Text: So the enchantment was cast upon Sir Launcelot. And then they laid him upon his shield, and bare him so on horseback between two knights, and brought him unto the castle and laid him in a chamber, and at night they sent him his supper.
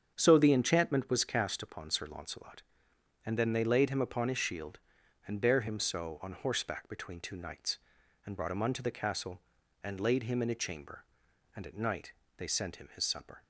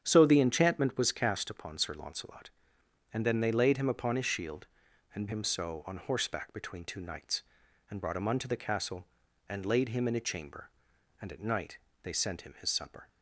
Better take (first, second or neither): first